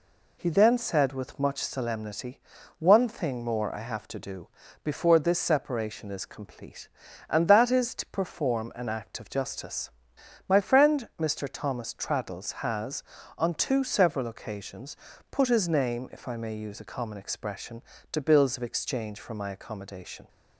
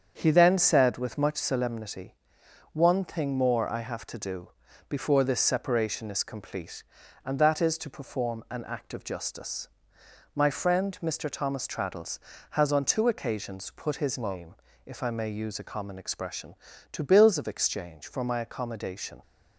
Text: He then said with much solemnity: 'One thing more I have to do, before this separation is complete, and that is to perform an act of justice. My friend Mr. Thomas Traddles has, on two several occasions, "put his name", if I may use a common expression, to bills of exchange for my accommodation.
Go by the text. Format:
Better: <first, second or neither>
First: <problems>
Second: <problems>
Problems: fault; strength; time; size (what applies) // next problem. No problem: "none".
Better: first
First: none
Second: starts louder than the rest; strong; until 1.1 s; 7.5 dB // skips "several"; at 13.0 s